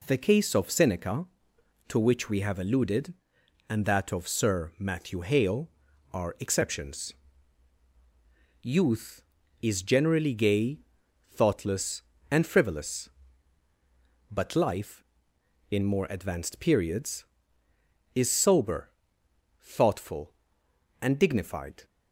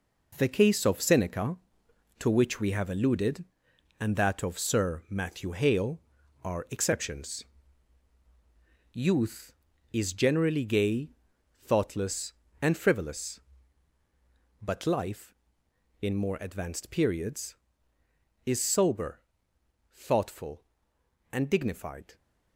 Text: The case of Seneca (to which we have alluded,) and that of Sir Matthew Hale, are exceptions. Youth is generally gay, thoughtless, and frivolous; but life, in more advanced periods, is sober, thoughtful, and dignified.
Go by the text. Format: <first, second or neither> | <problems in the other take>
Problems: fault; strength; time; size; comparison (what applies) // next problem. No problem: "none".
first | gets quieter; strong; throughout; 8.5 dB